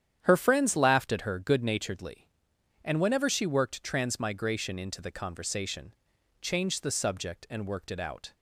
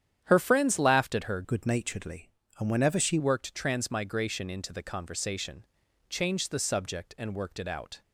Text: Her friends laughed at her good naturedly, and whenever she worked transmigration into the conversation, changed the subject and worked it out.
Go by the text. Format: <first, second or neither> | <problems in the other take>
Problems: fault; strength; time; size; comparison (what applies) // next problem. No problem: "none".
first | starts louder than the rest; strong; until 1.2 s; 9.5 dB; strong in the first // changes voice from "good" to "she"; from 1.4 to 3.1 s; 1.7 s long